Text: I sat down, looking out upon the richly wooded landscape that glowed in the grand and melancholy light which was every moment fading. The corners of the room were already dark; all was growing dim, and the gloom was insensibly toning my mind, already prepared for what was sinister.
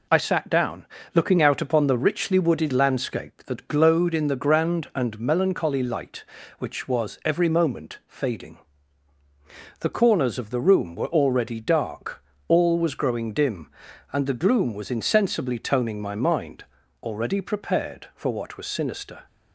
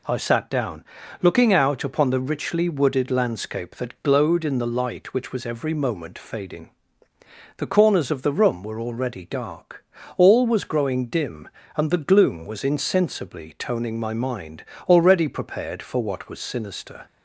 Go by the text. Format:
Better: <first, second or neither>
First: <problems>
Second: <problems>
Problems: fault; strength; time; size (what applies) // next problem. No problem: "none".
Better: first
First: none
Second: skips "grand and melancholy"; at 4.6 s